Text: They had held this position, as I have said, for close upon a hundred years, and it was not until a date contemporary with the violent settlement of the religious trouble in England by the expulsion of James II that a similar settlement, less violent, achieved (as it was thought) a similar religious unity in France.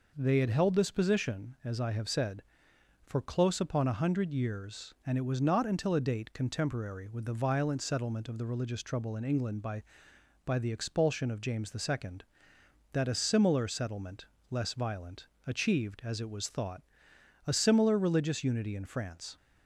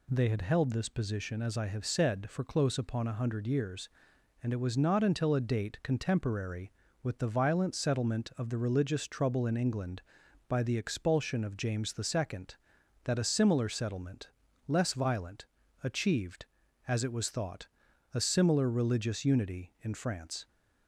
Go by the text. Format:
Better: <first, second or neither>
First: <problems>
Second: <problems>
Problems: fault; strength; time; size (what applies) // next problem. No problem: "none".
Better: second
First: says "by" twice; at 10.4 s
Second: none